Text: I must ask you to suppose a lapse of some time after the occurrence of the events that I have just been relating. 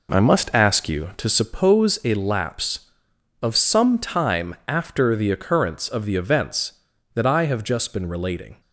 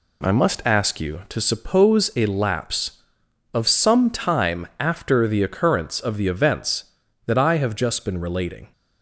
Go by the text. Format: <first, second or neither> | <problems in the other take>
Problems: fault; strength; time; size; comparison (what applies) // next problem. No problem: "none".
second | starts louder than the rest; noticeable; until 1.7 s; 4.5 dB